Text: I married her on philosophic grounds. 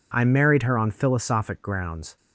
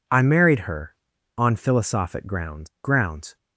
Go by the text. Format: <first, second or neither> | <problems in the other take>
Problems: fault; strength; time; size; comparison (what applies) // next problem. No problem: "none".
first | says "grounds" twice; at 2.8 s